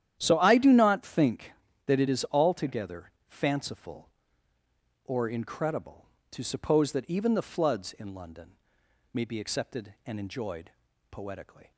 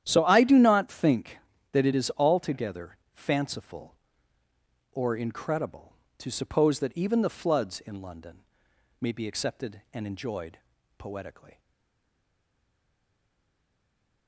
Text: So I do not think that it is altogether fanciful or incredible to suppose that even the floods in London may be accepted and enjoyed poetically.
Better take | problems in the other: first | starts louder than the rest; strong; until 1.0 s; 11 dB; strong in the first // pauses between "altogether" and "fanciful"; slight; at 2.9 s; 0.18 s long; slight in the first // pauses between "London" and "may"; noticeable; at 8.3 s; 0.62 s long; noticeable in the first // pauses between "enjoyed" and "poetically"; at 10.5 s; 0.40 s long; also in the first // stays silent after the last word; strong; from 11.5 s on; 2.7 s long

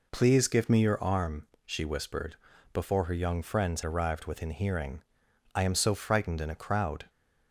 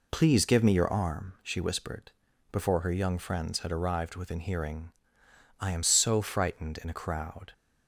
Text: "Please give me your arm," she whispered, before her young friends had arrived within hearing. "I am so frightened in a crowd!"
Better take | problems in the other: second | skips "had"; at 3.8 s

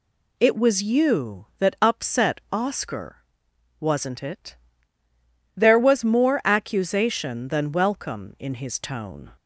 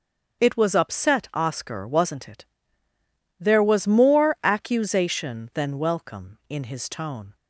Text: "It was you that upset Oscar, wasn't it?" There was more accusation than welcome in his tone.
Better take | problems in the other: first | starts louder than the rest; noticeable; until 1.4 s; 6 dB // skips "you that"; at 0.7 s

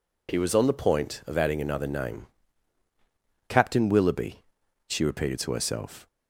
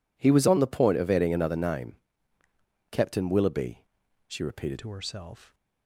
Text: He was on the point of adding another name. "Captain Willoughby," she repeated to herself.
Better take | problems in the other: first | changes voice at "to"; from 4.7 s on; 0.8 s long

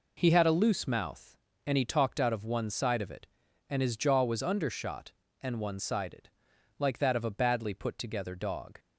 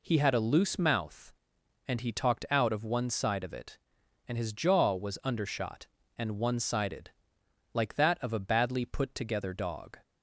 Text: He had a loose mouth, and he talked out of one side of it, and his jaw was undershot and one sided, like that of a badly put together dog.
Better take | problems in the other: neither | none

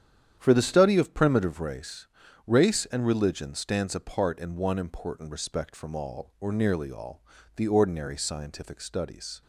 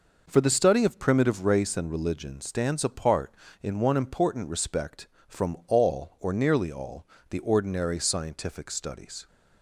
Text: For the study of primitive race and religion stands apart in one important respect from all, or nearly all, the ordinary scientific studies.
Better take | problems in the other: second | starts louder than the rest; strong; until 1.3 s; 9.5 dB // says "race" twice; at 2.4 s

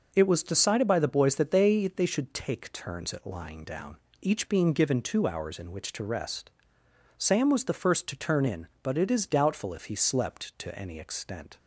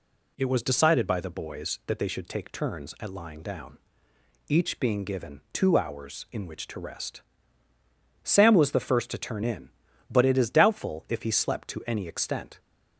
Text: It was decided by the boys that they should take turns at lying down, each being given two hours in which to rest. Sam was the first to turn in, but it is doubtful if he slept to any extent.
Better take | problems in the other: second | says "they" twice; at 1.8 s

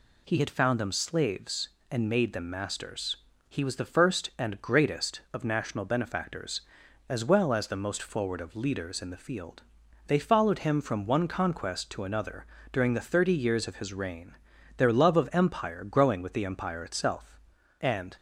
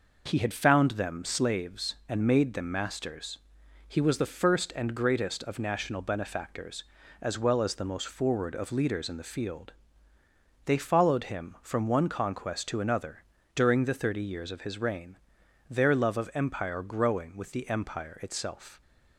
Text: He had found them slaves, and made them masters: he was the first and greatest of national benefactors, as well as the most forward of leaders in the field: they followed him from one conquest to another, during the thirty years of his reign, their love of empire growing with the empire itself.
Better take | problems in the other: second | goes on to say "And"; slight; from 17.8 s on; 0.34 s long

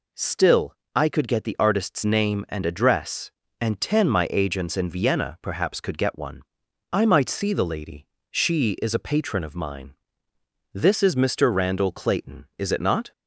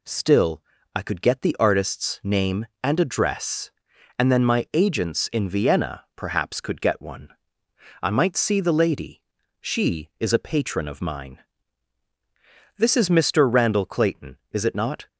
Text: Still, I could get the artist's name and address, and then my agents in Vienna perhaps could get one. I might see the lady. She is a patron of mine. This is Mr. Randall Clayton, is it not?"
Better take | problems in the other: second | says "ten" for "then"; at 3.7 s

